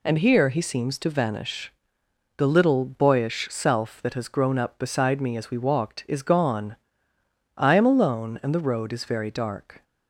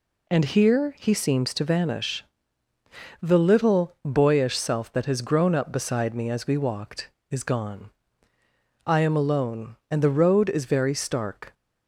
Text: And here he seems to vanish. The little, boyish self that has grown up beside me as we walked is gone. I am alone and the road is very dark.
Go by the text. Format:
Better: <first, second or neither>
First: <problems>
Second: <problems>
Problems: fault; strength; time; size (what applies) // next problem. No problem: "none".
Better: first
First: none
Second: says "stark" for "dark"; at 10.9 s